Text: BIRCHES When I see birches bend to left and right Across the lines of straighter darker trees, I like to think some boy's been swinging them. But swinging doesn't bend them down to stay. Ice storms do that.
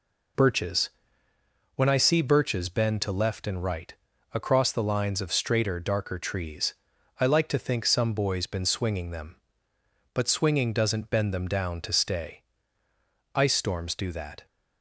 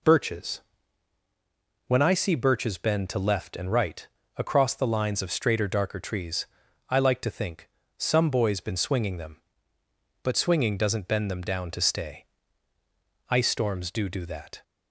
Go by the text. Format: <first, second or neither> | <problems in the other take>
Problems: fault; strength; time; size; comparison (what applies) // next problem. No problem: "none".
first | pauses between "BIRCHES" and "When"; at 0.6 s; 1.2 s long; noticeable in the first // pauses between "right" and "Across"; slight; at 4.0 s; 0.32 s long; also in the first // pauses between "think" and "some"; slight; at 7.6 s; 0.30 s long // says "do" twice; at 14.0 s